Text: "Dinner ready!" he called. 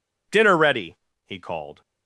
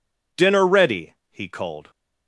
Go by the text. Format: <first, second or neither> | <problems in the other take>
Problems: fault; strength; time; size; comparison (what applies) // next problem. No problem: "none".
neither | none